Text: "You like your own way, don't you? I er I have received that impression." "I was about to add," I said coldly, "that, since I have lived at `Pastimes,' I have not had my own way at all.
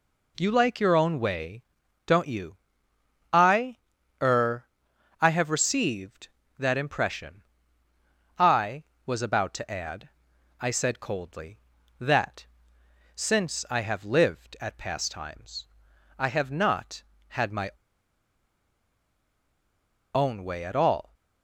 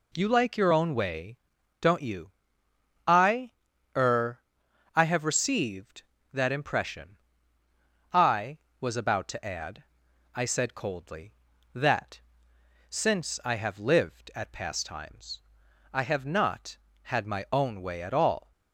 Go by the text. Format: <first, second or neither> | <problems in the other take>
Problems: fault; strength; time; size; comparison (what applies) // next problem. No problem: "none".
second | pauses between "I" and "er"; at 3.7 s; 0.44 s long; also in the second // pauses between "er" and "I"; noticeable; at 4.6 s; 0.54 s long; noticeable in the second // pauses between "my" and "own"; strong; at 17.7 s; 2.4 s long